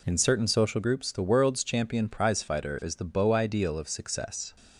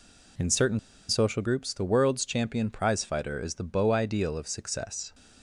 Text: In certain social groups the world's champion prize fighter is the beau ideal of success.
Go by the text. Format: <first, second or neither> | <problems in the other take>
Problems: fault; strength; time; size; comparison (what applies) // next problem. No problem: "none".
first | pauses between "certain" and "social"; slight; at 0.7 s; 0.29 s long